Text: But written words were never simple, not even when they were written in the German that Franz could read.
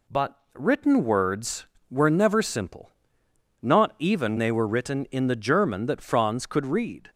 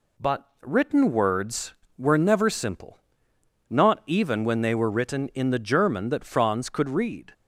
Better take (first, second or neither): second